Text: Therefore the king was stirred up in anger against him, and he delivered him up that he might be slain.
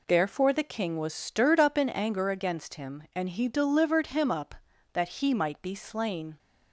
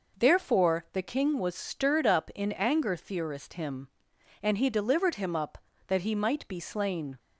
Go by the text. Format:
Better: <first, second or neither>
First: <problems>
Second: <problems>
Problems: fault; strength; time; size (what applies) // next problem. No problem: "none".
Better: first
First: none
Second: says "theorist" for "against"; at 2.9 s